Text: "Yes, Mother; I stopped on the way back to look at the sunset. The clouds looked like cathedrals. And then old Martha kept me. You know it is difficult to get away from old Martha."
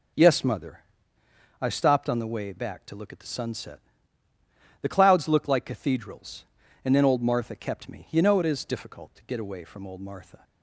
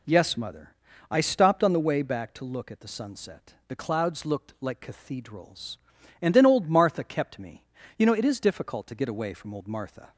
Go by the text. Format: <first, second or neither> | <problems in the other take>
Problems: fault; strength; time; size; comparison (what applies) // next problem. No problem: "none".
neither | none